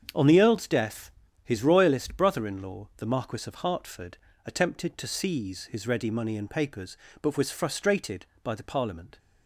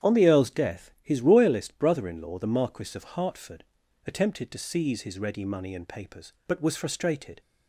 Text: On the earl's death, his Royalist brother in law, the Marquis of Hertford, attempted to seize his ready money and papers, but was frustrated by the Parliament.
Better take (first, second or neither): first